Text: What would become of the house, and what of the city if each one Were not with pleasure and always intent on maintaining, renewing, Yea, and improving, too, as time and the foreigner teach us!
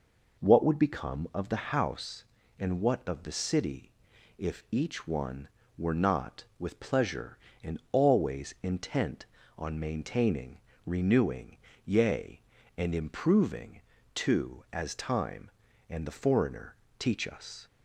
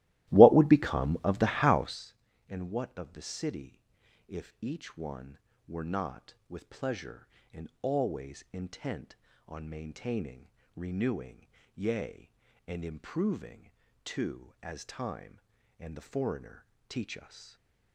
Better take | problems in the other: first | starts louder than the rest; strong; until 2.1 s; 16.5 dB // pauses between "city" and "if"; noticeable; at 3.7 s; 0.48 s long; noticeable in the first // pauses between "foreigner" and "teach"; slight; at 16.6 s; 0.24 s long; slight in the first // stays silent after the last word; slight; from 17.3 s on; 0.6 s long

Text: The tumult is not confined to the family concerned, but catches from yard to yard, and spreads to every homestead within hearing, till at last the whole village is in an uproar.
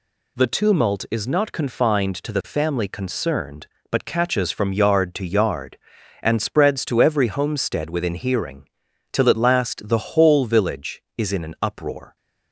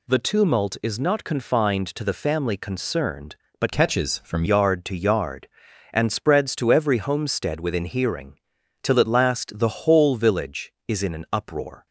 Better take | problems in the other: first | changes voice from "catches" to "from"; from 3.7 to 4.4 s; 0.7 s long

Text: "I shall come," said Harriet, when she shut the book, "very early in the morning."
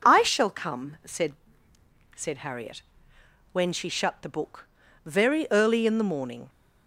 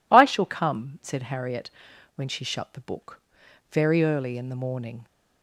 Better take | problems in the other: second | says "said" twice; at 2.1 s

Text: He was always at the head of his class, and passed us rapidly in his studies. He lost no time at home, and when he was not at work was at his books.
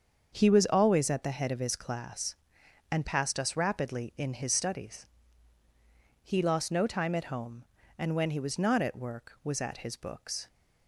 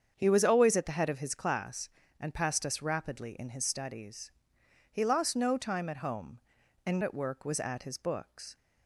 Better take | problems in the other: first | starts louder than the rest; strong; until 1.1 s; 7.5 dB; also in the first // skips "when he was not"; at 7.0 s

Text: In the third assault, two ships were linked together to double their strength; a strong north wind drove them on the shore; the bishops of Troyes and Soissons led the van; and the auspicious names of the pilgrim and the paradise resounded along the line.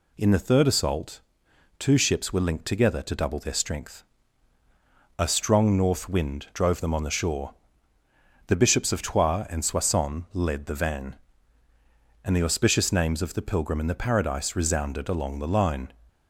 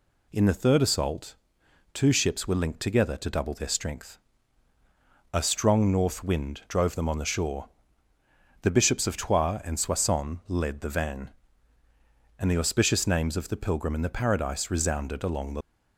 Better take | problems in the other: first | stops before "line"; at 15.6 s

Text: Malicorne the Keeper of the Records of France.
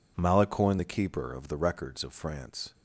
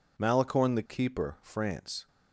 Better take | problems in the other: first | skips "of the Records of"; at 1.3 s

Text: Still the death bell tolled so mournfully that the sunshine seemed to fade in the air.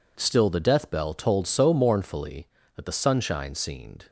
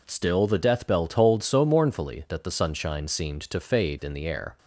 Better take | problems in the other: second | stops before "to fade in the air"; at 4.0 s

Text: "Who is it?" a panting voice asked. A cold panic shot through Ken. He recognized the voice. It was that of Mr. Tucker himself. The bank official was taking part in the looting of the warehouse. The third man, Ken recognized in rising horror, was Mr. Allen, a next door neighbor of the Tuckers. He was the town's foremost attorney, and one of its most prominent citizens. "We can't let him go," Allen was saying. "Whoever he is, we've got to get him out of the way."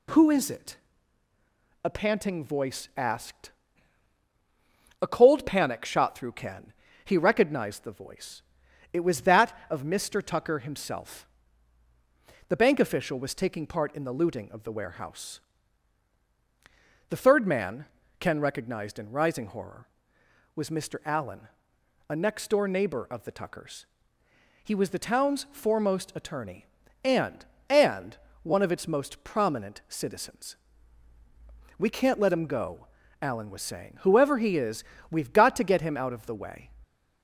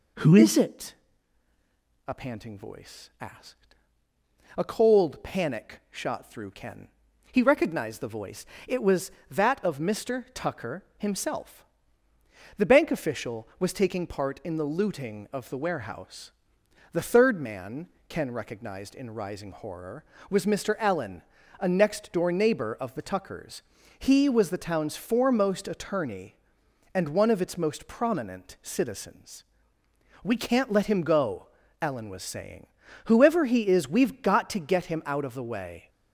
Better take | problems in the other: second | says "and" twice; at 27.6 s

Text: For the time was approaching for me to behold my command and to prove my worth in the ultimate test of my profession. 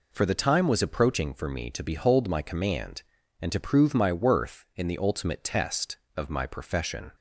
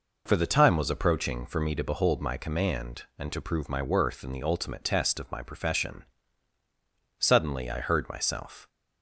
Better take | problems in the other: first | goes on to say "Suddenly I heard myself"; from 7.1 s on; 1.4 s long

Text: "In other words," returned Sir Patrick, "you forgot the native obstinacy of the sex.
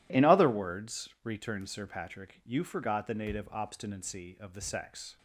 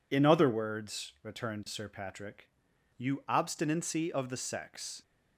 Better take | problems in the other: first | skips "forgot the native"; at 3.2 s

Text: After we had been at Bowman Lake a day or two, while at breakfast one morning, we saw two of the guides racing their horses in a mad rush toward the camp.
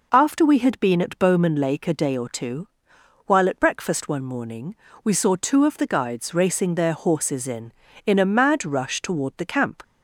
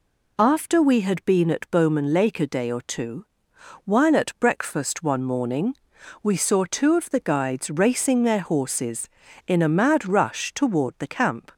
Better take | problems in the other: second | says "in" twice; at 8.0 s

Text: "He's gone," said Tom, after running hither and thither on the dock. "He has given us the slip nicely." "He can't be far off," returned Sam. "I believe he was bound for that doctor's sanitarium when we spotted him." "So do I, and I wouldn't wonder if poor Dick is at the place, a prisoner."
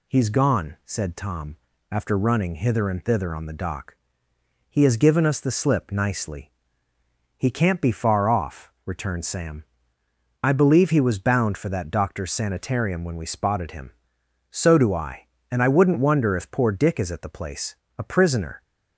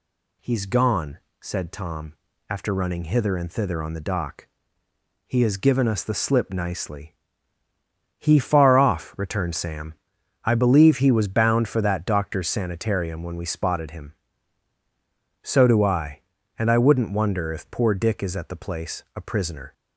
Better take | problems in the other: first | skips "can't be"; at 8.3 s

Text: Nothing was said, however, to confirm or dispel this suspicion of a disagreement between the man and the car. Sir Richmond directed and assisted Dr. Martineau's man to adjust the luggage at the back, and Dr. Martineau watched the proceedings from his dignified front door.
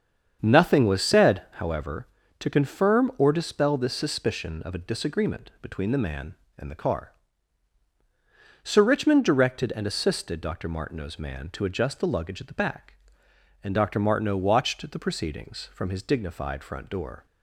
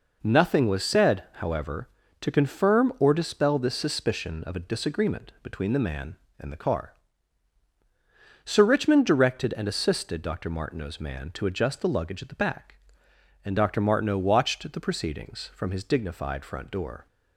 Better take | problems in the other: second | starts louder than the rest; strong; until 1.5 s; 7.5 dB

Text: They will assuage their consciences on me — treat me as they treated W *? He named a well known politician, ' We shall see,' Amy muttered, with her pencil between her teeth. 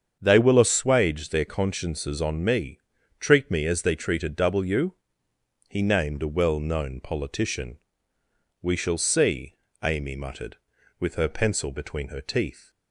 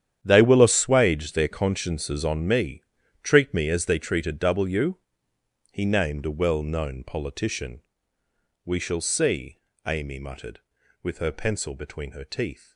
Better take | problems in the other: first | gets quieter; strong; throughout; 17.5 dB // starts louder than the rest; strong; until 1.2 s; 9.5 dB; strong in the first

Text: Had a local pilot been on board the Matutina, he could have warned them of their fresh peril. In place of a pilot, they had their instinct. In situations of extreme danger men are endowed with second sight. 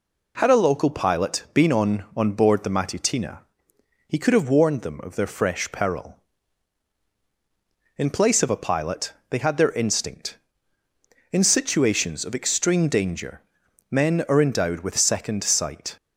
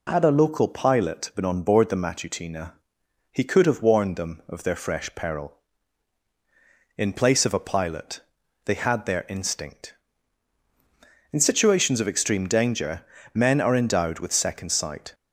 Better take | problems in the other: second | says "on" twice; at 2.1 s // pauses between "danger" and "men"; noticeable; at 13.4 s; 0.50 s long; slight in the second

